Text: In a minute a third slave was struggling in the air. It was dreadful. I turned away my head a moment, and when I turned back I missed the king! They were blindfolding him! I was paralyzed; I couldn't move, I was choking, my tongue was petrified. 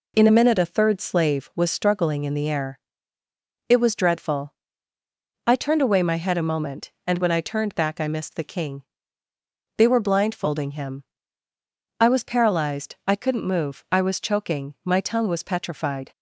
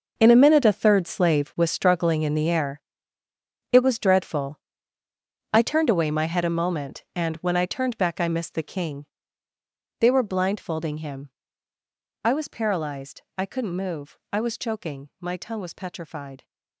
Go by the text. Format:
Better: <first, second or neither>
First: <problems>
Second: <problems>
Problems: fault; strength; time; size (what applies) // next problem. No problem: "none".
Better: first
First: none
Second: gets quieter; strong; throughout; 13 dB